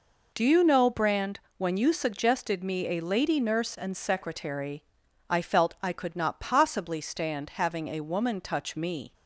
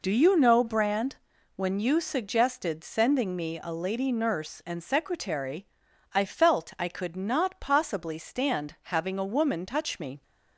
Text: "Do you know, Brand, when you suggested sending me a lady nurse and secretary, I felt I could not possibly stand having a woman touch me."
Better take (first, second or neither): second